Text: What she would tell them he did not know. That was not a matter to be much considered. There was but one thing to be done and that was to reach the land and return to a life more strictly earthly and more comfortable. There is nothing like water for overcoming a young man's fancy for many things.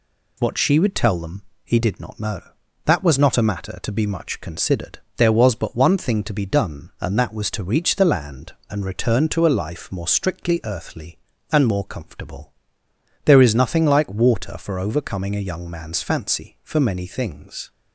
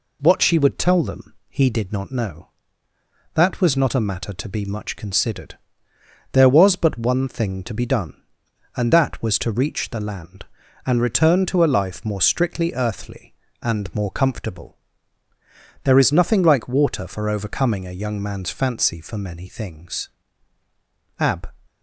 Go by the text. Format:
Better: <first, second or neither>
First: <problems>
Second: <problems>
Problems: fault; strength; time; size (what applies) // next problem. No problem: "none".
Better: first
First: pauses between "them" and "he"; slight; at 1.4 s; 0.22 s long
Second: pauses between "them" and "he"; slight; at 1.3 s; 0.16 s long // goes on to say "Ab"; slight; from 21.1 s on; 0.30 s long